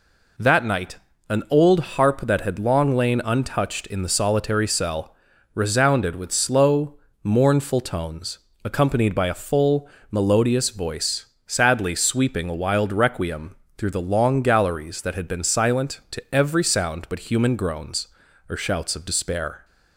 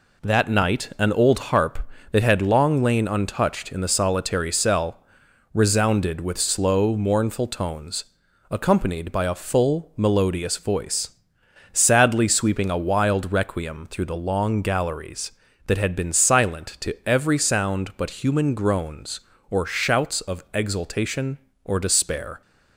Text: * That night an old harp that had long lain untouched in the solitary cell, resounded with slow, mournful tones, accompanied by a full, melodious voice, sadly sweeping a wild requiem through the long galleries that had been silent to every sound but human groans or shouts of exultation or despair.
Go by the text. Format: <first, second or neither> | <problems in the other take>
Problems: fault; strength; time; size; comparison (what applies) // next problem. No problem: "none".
second | pauses between "night" and "an"; slight; at 0.9 s; 0.30 s long // pauses between "requiem" and "through"; slight; at 13.5 s; 0.24 s long // skips "exultation or"; at 19.0 s